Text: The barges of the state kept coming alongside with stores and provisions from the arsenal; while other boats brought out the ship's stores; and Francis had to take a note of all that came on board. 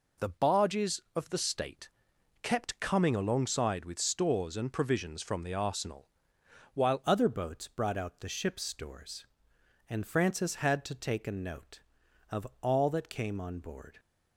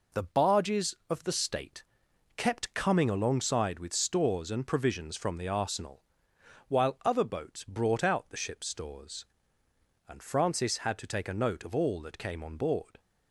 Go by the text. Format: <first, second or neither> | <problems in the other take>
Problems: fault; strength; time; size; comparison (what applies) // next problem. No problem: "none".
second | pauses between "state" and "kept"; noticeable; at 1.8 s; 0.52 s long; noticeable in the second // changes voice at "other"; from 7.0 s on; 6.9 s long